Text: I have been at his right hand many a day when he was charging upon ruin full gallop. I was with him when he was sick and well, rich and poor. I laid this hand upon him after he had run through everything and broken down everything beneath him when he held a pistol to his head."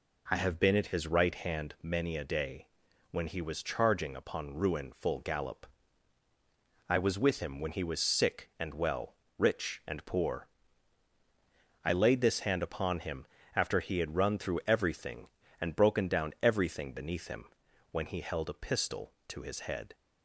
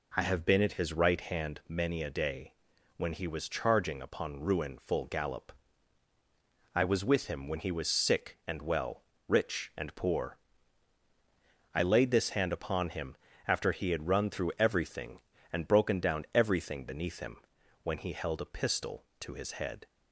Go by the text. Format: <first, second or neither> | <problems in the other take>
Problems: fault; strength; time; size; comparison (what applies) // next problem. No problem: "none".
neither | pauses between "day" and "when"; the same in both // pauses between "him" and "after"; slight; the same in both // pauses between "him" and "when"; the same in both